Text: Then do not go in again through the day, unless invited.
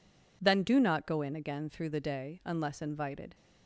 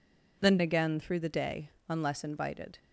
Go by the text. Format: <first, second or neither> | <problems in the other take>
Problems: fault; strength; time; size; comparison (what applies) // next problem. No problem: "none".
first | skips "do not go in"; at 0.5 s